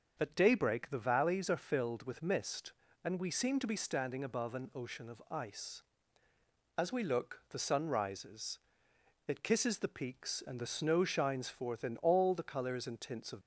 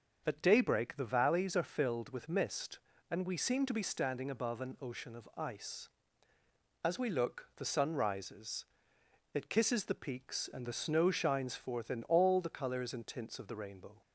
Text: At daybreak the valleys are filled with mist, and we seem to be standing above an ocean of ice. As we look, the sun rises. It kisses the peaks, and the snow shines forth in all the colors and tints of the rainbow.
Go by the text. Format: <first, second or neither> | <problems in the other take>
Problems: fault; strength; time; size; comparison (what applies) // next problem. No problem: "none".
second | starts louder than the rest; until 1.1 s; 6.5 dB; also in the second // stops before "the rainbow"; at 13.4 s